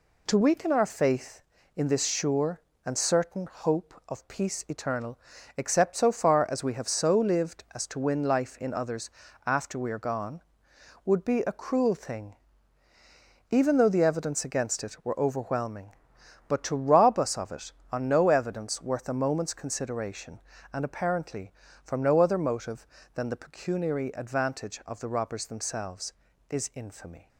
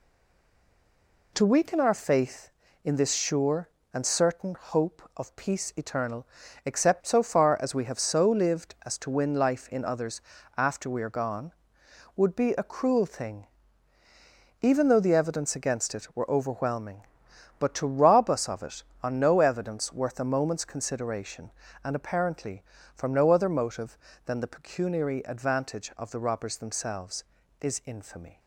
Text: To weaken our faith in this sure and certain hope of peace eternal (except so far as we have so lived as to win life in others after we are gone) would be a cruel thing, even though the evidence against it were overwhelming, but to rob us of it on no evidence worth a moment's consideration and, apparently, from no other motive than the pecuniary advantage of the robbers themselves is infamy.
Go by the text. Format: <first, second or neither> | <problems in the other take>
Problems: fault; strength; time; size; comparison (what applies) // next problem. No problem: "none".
first | stays silent before the first word; noticeable; until 1.3 s; 1.3 s long // pauses between "others" and "after"; at 10.1 s; 0.38 s long; also in the first